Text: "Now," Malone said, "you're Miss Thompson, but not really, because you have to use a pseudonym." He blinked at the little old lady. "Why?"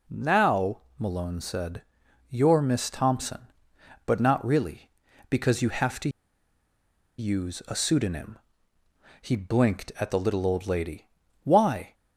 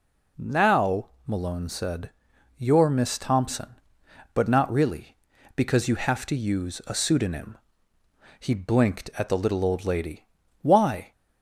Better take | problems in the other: second | pauses between "to" and "use"; at 6.0 s; 1.1 s long

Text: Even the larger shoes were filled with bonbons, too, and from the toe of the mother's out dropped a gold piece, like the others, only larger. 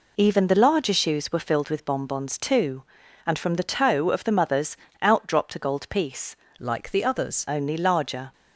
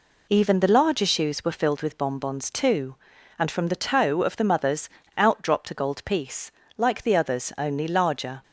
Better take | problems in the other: second | pauses between "mother's" and "out"; slight; at 4.7 s; 0.24 s long; slight in the second // changes voice from "like" to "others"; from 6.5 to 7.4 s; 0.9 s long

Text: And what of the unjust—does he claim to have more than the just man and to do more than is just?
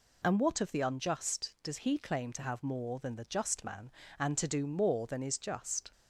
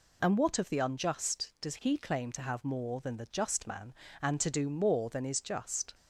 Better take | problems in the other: neither | none

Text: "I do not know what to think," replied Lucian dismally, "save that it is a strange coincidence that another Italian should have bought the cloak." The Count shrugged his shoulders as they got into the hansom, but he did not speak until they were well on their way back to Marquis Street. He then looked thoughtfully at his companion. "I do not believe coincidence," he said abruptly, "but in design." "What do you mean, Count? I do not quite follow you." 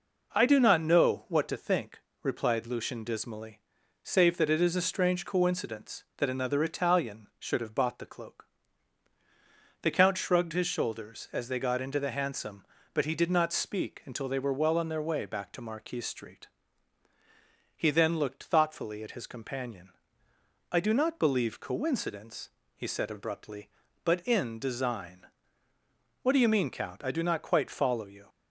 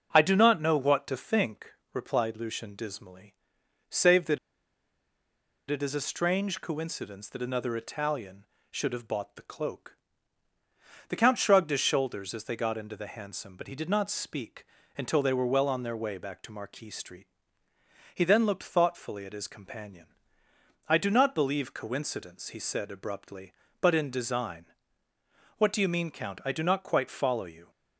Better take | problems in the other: first | starts louder than the rest; until 1.1 s; 6 dB // pauses between "that" and "it"; strong; at 4.3 s; 1.3 s long // pauses between "speak" and "until"; slight; at 14.6 s; 0.32 s long

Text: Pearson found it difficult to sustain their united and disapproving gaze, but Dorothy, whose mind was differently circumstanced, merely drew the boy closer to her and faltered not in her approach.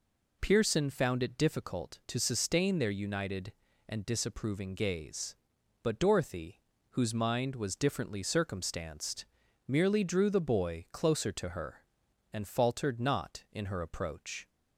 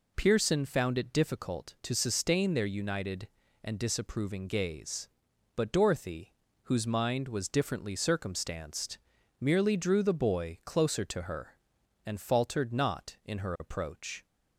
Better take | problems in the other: neither | none

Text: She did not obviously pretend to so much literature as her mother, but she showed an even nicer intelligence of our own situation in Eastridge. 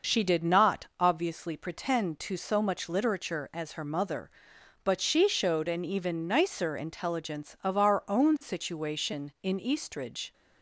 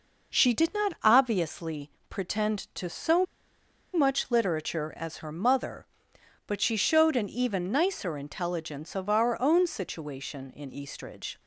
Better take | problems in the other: first | pauses between "obviously" and "pretend"; slight; at 1.9 s; 0.16 s long // pauses between "so" and "much"; noticeable; at 3.2 s; 0.70 s long

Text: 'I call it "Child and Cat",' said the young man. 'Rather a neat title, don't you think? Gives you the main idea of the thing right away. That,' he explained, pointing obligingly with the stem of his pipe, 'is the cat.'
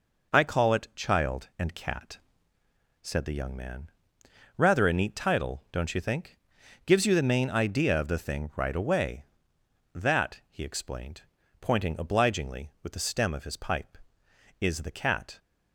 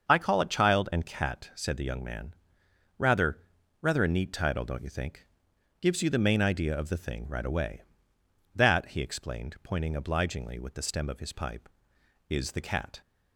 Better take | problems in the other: first | starts louder than the rest; until 1.1 s; 6.5 dB // says "Rather" twice; at 3.8 s

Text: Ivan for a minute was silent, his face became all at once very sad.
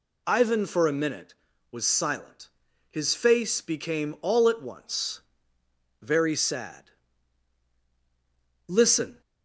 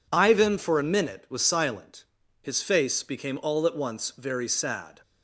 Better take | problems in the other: second | pauses between "once" and "very"; noticeable; at 5.2 s; 0.78 s long // goes on to say "Listen"; from 8.6 s on; 0.54 s long

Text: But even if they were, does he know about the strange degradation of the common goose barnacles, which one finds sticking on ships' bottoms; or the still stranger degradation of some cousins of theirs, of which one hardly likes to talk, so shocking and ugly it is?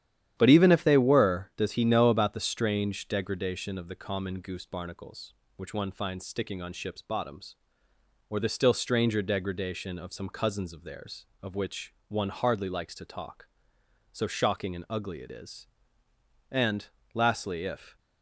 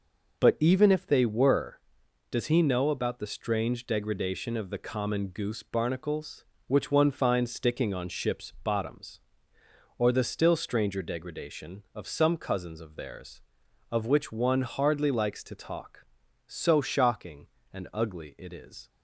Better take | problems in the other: second | starts louder than the rest; strong; until 1.3 s; 10.5 dB // pauses between "which" and "one"; slight; at 11.9 s; 0.16 s long // goes on to say "And lastly if"; from 16.5 s on; 1.4 s long

